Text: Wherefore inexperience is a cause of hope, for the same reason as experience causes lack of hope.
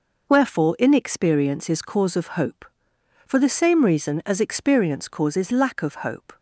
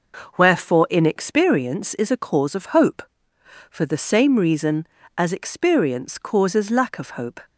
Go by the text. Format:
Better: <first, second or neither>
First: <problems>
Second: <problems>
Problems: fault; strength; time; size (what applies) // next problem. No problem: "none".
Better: second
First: skips "a"; at 1.8 s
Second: none